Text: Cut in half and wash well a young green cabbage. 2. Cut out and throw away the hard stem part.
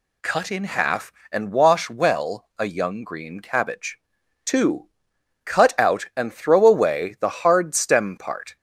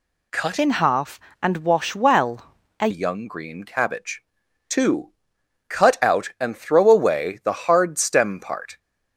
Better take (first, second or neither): first